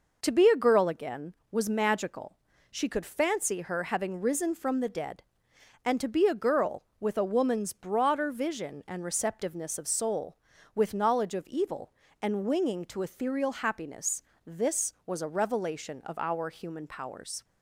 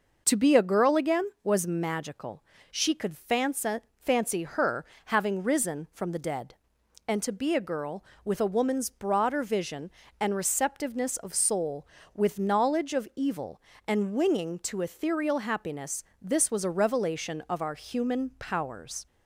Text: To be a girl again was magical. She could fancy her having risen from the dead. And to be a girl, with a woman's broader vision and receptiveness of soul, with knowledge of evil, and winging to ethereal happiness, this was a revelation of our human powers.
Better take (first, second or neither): first